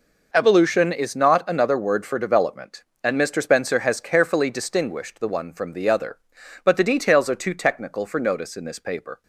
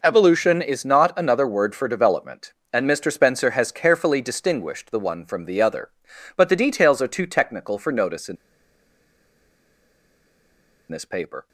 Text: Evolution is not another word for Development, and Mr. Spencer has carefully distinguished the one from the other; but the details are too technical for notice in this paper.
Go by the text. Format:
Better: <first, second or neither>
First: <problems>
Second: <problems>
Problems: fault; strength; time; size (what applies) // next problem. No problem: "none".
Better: first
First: none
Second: pauses between "in" and "this"; strong; at 8.3 s; 2.5 s long